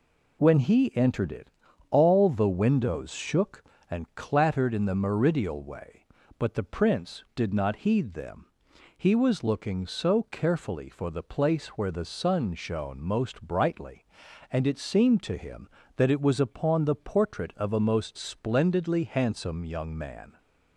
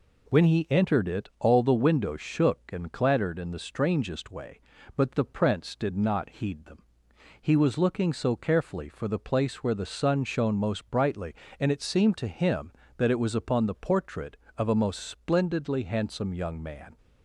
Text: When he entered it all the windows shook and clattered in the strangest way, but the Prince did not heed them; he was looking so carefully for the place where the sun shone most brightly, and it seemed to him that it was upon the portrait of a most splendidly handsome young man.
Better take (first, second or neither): second